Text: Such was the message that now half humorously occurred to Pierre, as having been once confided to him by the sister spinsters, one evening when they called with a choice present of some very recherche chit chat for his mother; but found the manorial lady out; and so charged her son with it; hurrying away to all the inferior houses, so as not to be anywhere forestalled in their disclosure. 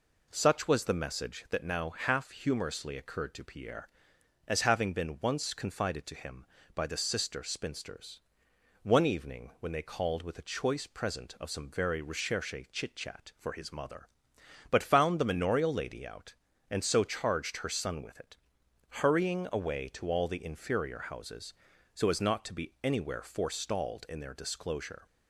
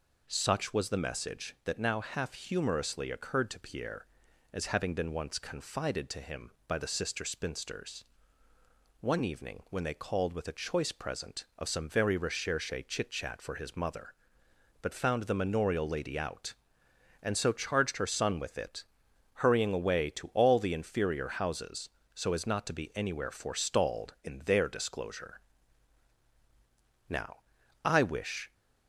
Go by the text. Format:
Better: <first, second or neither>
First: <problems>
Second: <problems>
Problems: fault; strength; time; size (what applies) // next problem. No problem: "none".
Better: first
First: none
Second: pauses between "recherche" and "chit"; slight; at 12.7 s; 0.16 s long // goes on to say "Now I wish"; from 27.0 s on; 1.4 s long